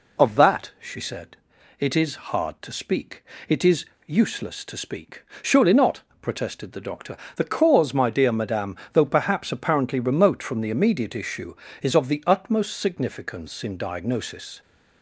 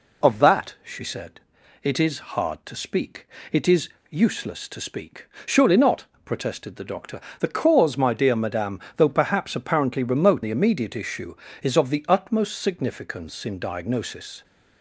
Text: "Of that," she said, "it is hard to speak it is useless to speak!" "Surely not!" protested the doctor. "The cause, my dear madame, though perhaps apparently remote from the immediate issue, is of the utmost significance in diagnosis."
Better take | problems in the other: first | pauses between "speak" and "it"; slight; at 3.2 s; 0.24 s long; slight in the first // pauses between "is" and "useless"; slight; at 3.8 s; 0.20 s long; slight in the first // skips "from"; at 10.4 s

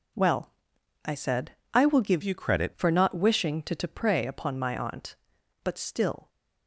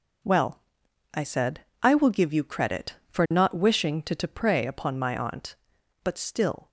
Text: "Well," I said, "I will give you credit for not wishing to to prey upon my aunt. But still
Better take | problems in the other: second | changes voice from "you" to "credit"; from 2.2 to 2.7 s; 0.5 s long

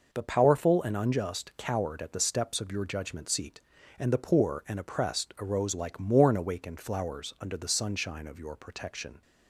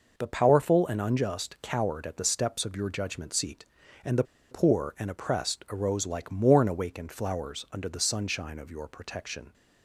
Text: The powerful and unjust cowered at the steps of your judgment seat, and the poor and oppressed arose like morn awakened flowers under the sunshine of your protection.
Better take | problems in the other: first | pauses between "the" and "poor"; slight; at 4.2 s; 0.27 s long

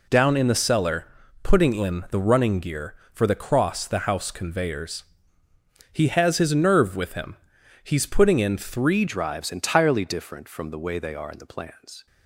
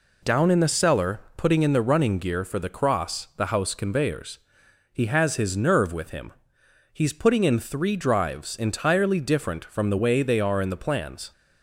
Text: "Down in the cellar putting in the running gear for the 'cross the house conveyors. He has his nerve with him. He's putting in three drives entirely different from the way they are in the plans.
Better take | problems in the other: second | pauses between "cellar" and "putting"; slight; at 1.0 s; 0.36 s long; slight in the second // changes voice at "drives"; from 9.0 s on; 3.0 s long

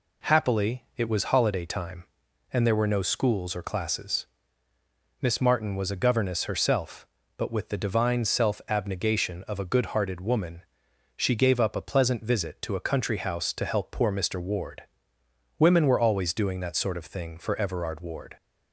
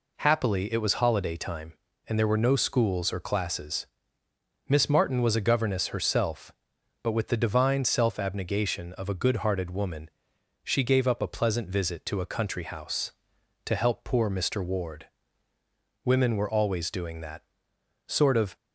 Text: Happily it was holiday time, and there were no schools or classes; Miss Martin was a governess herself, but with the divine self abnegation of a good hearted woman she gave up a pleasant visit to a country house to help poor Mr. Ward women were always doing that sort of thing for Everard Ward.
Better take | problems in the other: first | pauses between "woman" and "she"; noticeable; at 10.0 s; 0.54 s long; noticeable in the first // pauses between "Ward" and "women"; noticeable; at 15.0 s; 0.98 s long; noticeable in the first // pauses between "that" and "sort"; noticeable; at 17.4 s; 0.64 s long // stops before "thing for Everard Ward"; at 18.5 s

